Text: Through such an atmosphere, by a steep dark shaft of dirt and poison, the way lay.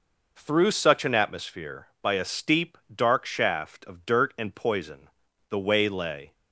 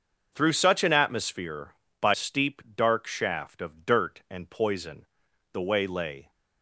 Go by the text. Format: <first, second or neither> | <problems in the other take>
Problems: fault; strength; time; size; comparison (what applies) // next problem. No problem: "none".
first | starts louder than the rest; until 1.3 s; 6.5 dB // skips "a"; at 2.1 s // pauses between "steep" and "dark"; slight; at 2.5 s; 0.16 s long; slight in the first